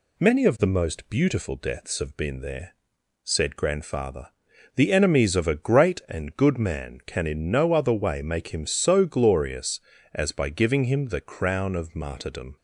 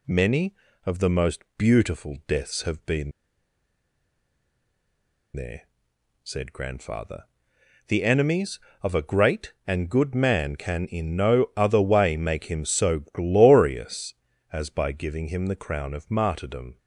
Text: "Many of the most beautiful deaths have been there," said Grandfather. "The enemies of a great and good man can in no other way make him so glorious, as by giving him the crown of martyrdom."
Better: first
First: none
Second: pauses between "been" and "there"; strong; at 3.1 s; 2.2 s long

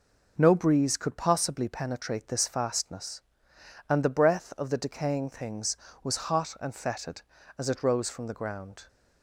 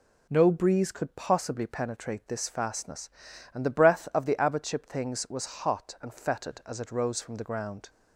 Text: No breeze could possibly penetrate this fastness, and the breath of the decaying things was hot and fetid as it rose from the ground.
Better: first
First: none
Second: says "abbotship" for "decaying"; at 4.3 s

